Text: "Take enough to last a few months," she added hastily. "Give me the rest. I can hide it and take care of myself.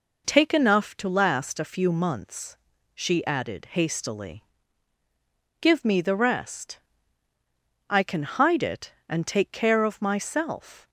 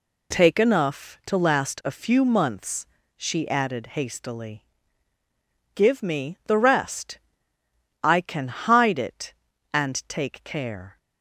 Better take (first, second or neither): first